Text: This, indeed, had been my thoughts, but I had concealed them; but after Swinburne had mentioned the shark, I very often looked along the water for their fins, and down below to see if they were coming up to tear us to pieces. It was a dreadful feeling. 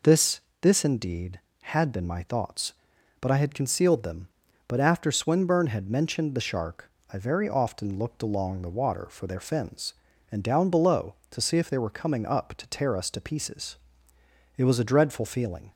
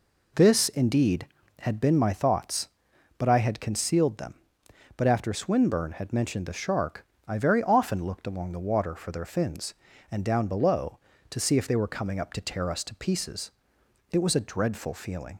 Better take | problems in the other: second | says "This" twice; at 0.6 s

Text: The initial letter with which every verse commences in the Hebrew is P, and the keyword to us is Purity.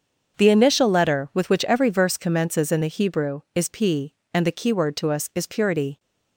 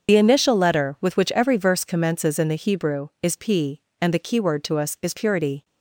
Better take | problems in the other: first | loses the start of "The"; at 0.0 s; 55 ms // starts louder than the rest; until 1.1 s; 6.5 dB; also in the first

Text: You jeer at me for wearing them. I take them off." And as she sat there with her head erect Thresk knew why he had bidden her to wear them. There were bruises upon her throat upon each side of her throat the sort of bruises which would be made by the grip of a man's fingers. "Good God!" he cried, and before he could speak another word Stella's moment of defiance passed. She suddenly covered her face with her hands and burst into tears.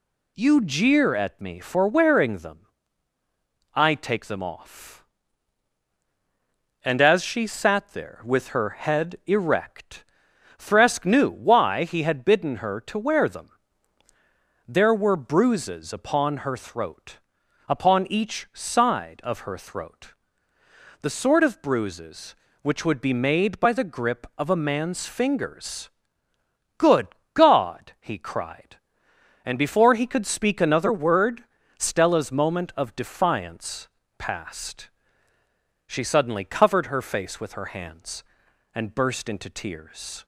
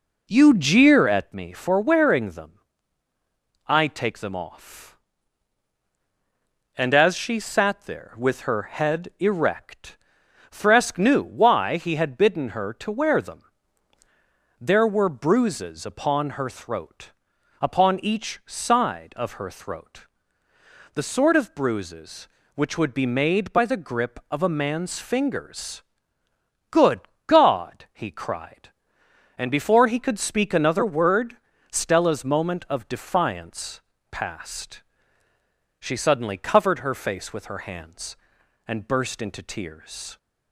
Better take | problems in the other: first | starts louder than the rest; until 1.4 s; 4 dB // pauses between "erect" and "Thresk"; noticeable; at 9.9 s; 0.54 s long; noticeable in the first // pauses between "throat" and "upon"; noticeable; at 17.1 s; 0.48 s long; noticeable in the first // pauses between "throat" and "the"; noticeable; at 20.0 s; 0.88 s long; noticeable in the first // pauses between "Good" and "God"; slight; at 27.0 s; 0.26 s long; slight in the first // pauses between "word" and "Stella's"; slight; at 31.3 s; 0.34 s long; slight in the first // pauses between "defiance" and "passed"; slight; at 33.8 s; 0.28 s long; slight in the first

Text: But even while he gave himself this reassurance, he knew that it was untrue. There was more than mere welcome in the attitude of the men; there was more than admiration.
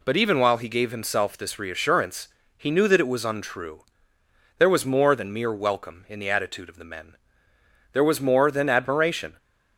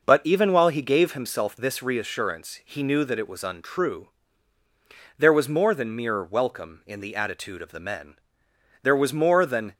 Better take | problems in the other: first | stops before "admiration"; at 9.7 s

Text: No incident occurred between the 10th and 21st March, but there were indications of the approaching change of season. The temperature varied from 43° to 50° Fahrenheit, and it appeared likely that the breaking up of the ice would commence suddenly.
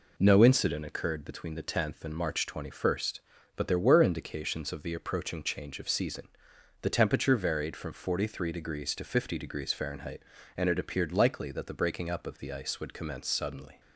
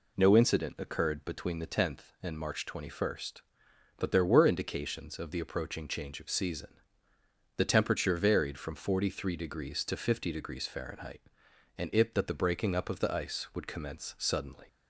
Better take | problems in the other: first | skips "appeared likely"; at 12.1 s

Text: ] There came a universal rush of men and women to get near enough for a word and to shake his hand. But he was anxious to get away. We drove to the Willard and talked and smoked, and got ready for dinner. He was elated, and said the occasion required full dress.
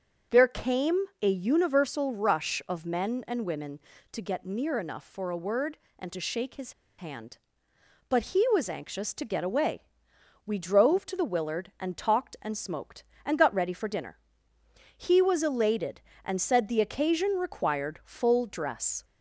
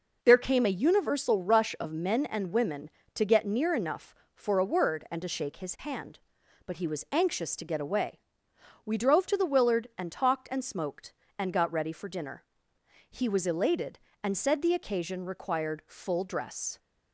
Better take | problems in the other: second | pauses between "came" and "a"; slight; at 1.0 s; 0.18 s long // pauses between "his" and "hand"; slight; at 6.7 s; 0.25 s long

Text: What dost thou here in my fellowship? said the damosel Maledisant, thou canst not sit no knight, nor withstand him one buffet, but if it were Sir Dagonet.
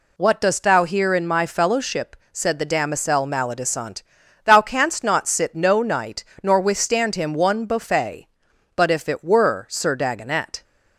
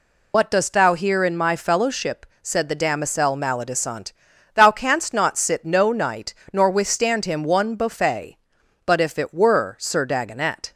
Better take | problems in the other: first | loses the start of "What"; at 0.3 s; 75 ms

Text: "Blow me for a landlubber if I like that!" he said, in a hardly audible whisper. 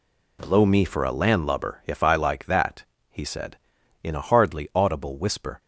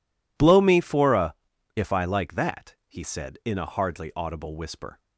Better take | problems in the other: first | skips "landlubber"; at 1.5 s

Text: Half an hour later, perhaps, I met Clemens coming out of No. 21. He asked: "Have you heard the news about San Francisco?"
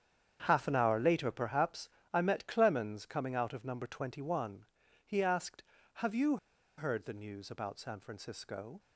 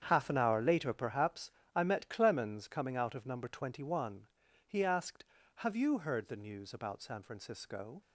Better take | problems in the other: second | starts louder than the rest; strong; until 1.4 s; 8 dB; strong in the second // pauses between "you" and "heard"; at 6.3 s; 0.40 s long

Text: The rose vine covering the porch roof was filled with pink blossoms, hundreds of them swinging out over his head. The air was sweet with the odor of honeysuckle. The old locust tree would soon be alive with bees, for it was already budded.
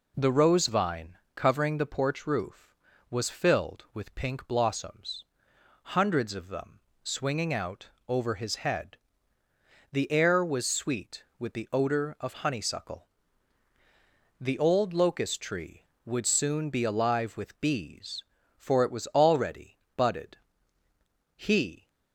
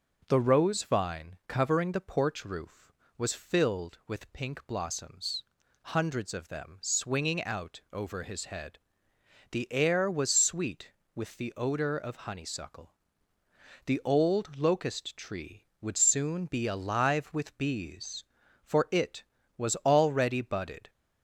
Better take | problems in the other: second | pauses between "vine" and "covering"; slight; at 1.1 s; 0.18 s long // pauses between "them" and "swinging"; slight; at 6.7 s; 0.24 s long // pauses between "out" and "over"; slight; at 7.8 s; 0.18 s long // pauses between "already" and "budded"; slight; at 19.7 s; 0.22 s long // goes on to say "He"; from 21.3 s on; 0.54 s long

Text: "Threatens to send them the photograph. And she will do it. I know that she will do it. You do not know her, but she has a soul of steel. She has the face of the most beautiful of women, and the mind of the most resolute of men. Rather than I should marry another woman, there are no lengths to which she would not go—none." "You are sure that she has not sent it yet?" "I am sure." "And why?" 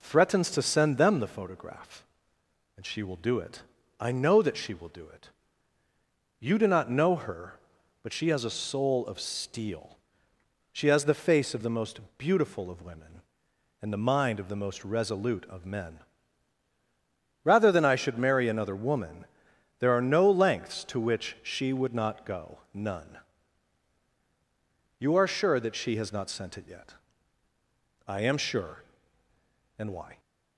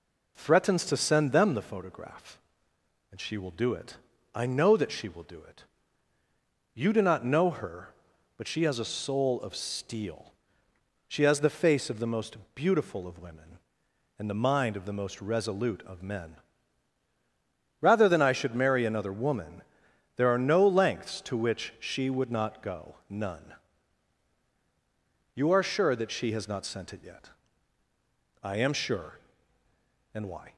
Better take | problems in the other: neither | pauses between "most" and "beautiful"; slight; the same in both

